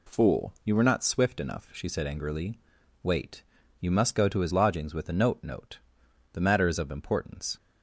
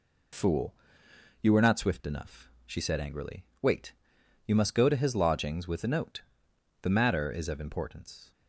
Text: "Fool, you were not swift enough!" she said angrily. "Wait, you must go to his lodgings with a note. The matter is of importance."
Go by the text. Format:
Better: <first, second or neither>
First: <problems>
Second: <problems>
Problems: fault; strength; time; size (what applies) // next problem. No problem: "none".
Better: second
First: says "note" twice; at 5.4 s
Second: none